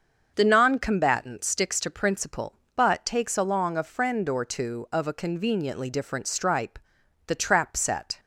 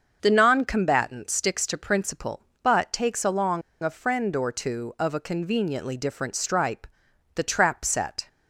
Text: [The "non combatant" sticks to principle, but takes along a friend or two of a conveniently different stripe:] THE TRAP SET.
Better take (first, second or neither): first